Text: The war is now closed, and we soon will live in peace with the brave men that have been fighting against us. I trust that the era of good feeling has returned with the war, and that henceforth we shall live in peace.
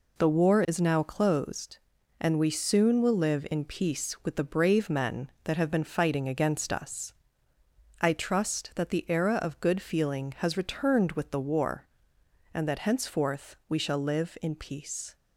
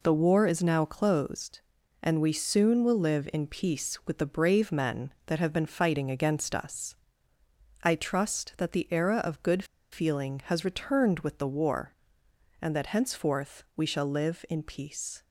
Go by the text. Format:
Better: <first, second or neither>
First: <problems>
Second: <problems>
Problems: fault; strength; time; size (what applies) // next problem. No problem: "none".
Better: first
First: none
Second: pauses between "good" and "feeling"; slight; at 9.6 s; 0.28 s long